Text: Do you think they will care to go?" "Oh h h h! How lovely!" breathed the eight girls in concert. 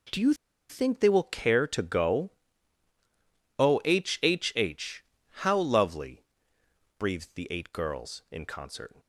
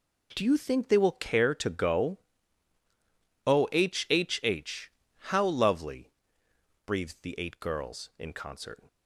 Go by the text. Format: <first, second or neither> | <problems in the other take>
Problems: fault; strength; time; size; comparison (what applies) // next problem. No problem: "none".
second | pauses between "you" and "think"; slight; at 0.3 s; 0.35 s long